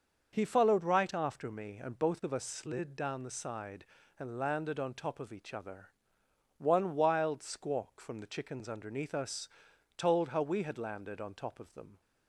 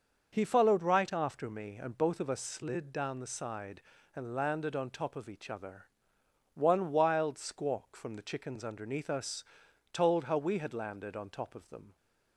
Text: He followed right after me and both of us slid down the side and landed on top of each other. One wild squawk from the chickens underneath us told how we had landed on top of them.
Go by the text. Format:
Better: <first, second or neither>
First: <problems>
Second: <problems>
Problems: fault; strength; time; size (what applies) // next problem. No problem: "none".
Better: neither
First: starts louder than the rest; until 1.3 s; 6 dB // pauses between "us" and "told"; noticeable; at 9.4 s; 0.48 s long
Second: starts louder than the rest; until 1.3 s; 6 dB // pauses between "us" and "told"; noticeable; at 9.4 s; 0.48 s long